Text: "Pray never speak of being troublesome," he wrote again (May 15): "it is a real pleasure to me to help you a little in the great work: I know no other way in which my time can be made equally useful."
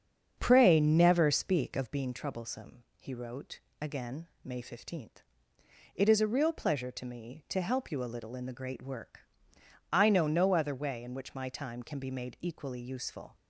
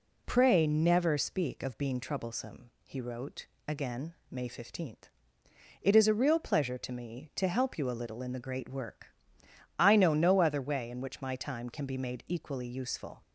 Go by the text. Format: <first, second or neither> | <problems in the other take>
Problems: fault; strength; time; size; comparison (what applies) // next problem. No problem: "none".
second | starts louder than the rest; strong; until 2.0 s; 7.5 dB // pauses between "wrote" and "again"; slight; at 3.5 s; 0.22 s long; slight in the second